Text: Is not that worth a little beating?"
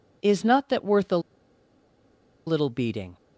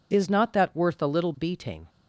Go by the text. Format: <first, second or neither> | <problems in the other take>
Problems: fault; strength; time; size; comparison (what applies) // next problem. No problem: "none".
second | pauses between "a" and "little"; strong; at 1.1 s; 1.2 s long